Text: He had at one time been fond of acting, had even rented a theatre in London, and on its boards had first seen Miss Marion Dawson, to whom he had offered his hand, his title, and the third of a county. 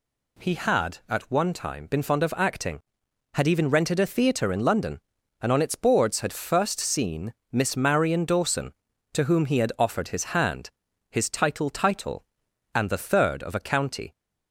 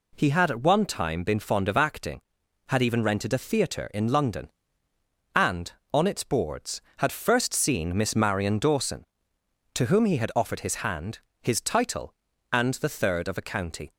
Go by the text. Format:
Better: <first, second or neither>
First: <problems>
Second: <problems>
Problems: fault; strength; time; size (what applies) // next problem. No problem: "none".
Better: second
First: pauses between "seen" and "Miss"; slight; at 7.3 s; 0.20 s long // says "title" twice; at 11.6 s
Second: none